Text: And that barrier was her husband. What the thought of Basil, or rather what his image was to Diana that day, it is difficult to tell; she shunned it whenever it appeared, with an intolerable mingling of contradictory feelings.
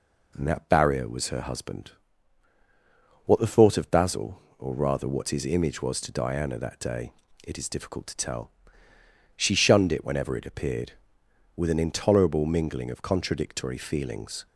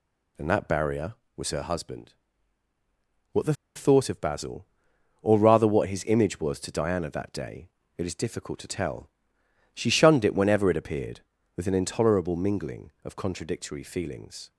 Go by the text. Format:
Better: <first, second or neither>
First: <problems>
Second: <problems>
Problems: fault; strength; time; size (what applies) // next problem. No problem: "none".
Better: first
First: none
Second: pauses between "the" and "thought"; slight; at 3.5 s; 0.20 s long